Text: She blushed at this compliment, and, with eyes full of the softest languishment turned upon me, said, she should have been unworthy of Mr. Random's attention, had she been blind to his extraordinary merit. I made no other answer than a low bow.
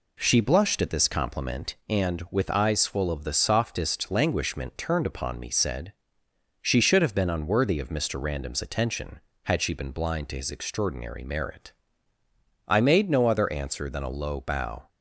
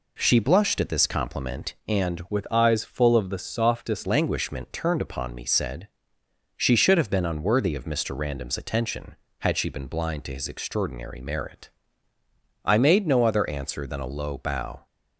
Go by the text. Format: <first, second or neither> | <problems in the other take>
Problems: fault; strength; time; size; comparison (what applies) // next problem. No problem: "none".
first | changes voice from "with" to "softest"; from 2.2 to 4.0 s; 1.8 s long